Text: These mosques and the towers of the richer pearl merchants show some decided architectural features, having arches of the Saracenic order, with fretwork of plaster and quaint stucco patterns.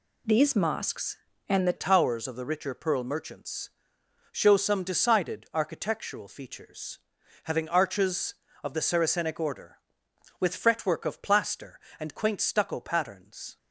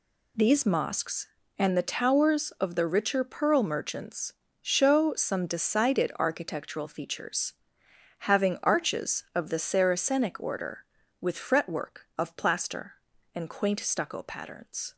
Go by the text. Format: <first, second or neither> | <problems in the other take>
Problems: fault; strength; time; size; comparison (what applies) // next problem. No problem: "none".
second | changes voice at "towers"; from 1.7 s on; 11.8 s long // pauses between "merchants" and "show"; noticeable; at 3.6 s; 0.62 s long; slight in the second